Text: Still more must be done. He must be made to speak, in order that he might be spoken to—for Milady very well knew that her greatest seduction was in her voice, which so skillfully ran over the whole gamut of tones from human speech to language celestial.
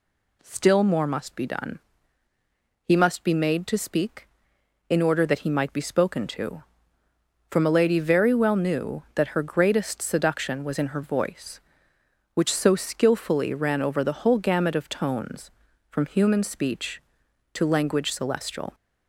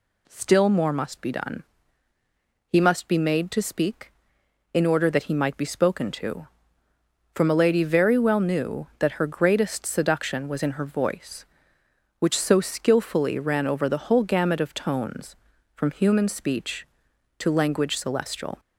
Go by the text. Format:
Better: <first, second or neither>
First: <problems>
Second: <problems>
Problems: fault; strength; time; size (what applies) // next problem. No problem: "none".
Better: neither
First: none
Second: none